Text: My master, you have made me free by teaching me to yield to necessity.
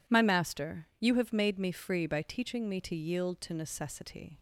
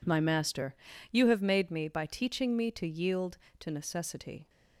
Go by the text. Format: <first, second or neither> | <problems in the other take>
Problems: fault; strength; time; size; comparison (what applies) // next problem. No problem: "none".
first | skips "free"; at 1.8 s